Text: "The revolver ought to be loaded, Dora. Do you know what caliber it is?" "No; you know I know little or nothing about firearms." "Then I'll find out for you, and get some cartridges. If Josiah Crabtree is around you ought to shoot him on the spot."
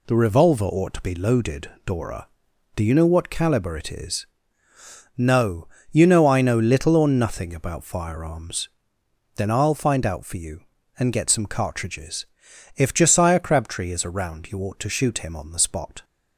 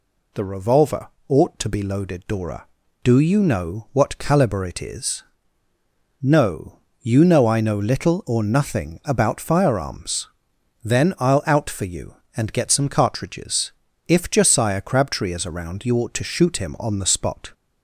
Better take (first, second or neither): first